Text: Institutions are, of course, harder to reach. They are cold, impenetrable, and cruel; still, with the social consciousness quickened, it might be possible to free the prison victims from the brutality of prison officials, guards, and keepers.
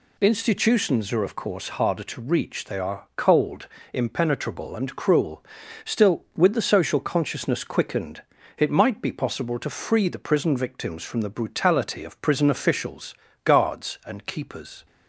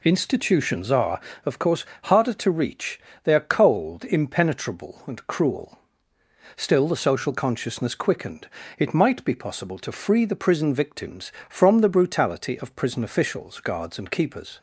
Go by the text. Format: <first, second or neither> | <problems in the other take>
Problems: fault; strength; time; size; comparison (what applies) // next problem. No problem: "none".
first | skips "with"; at 6.8 s